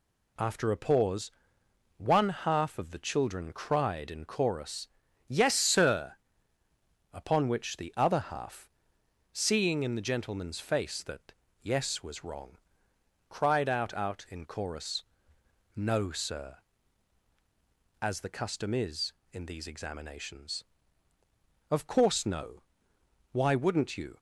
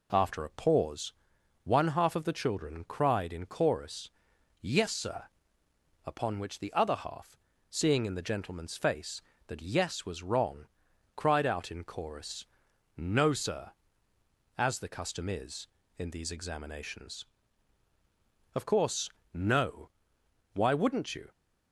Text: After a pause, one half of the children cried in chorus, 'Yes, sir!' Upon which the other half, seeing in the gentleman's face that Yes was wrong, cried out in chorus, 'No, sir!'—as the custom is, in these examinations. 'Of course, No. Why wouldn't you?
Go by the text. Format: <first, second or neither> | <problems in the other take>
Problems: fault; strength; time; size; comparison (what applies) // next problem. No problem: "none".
second | pauses between "that" and "Yes"; slight; at 11.3 s; 0.26 s long // says "out" twice; at 13.9 s